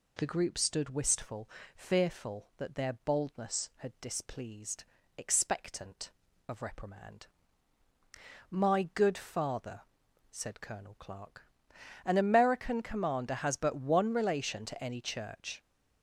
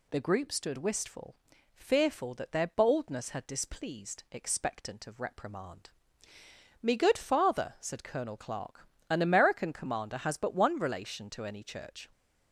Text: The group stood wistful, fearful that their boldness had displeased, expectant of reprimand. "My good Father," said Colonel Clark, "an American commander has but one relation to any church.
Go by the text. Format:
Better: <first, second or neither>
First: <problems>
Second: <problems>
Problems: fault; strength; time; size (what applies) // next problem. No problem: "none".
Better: first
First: none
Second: says "Me" for "My"; at 6.8 s